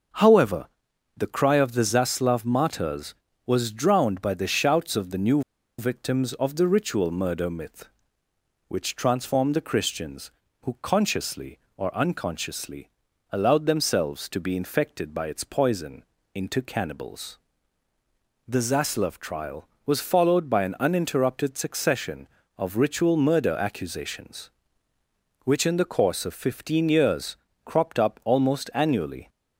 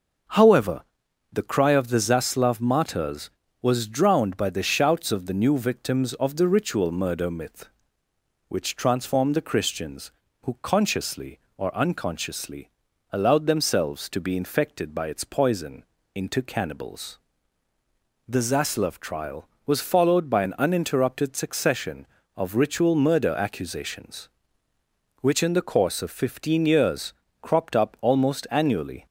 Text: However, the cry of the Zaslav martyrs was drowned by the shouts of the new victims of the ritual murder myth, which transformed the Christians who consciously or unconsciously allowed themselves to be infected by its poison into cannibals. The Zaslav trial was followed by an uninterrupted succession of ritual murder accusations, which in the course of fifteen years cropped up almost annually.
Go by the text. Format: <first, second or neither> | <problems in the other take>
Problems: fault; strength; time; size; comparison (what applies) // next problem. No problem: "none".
second | pauses between "new" and "victims"; at 5.4 s; 0.37 s long // pauses between "unconsciously" and "allowed"; at 12.8 s; 0.42 s long; also in the second // pauses between "poison" and "into"; slight; at 16.0 s; 0.28 s long; slight in the second // pauses between "years" and "cropped"; slight; at 27.3 s; 0.28 s long; slight in the second